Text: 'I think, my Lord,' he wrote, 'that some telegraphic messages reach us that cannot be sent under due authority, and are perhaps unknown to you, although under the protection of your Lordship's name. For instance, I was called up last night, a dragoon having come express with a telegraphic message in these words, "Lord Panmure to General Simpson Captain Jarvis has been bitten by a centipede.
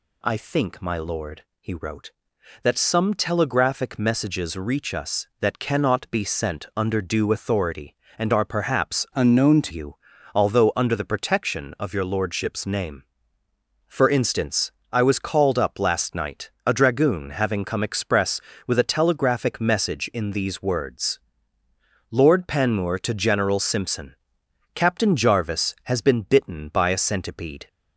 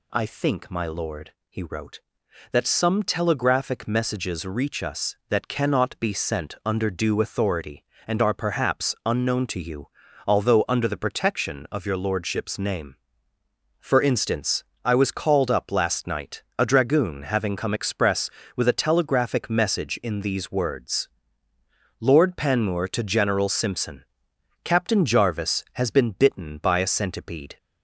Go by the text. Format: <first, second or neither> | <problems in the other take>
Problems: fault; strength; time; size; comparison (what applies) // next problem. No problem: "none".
second | changes voice from "unknown" to "to"; from 9.1 to 9.7 s; 0.6 s long // pauses between "Simpson" and "Captain"; noticeable; at 24.1 s; 0.58 s long; noticeable in the second